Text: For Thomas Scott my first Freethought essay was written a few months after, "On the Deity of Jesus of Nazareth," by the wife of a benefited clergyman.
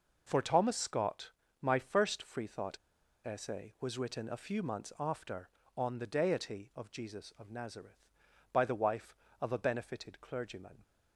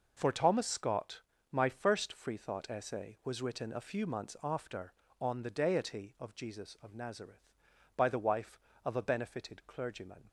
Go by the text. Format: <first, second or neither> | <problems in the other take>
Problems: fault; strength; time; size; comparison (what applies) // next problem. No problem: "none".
second | pauses between "Scott" and "my"; slight; at 1.3 s; 0.30 s long; slight in the second // pauses between "Freethought" and "essay"; noticeable; at 2.7 s; 0.46 s long